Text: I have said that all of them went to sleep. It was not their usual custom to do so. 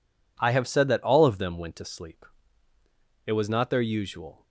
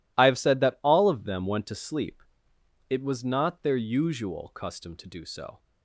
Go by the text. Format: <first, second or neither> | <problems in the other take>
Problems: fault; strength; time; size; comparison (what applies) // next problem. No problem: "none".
second | stops before "custom to do so"; at 4.4 s